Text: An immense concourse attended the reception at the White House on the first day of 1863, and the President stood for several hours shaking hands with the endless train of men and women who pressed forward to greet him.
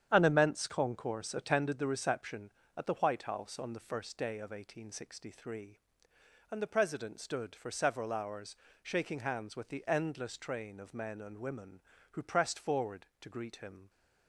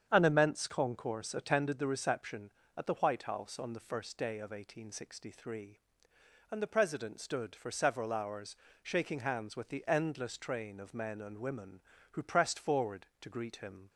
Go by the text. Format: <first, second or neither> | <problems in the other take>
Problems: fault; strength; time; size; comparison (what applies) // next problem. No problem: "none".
second | gets quieter; strong; throughout; 8 dB // starts louder than the rest; strong; until 1.1 s; 9 dB; strong in the second // pauses between "hours" and "shaking"; slight; at 8.5 s; 0.26 s long; slight in the second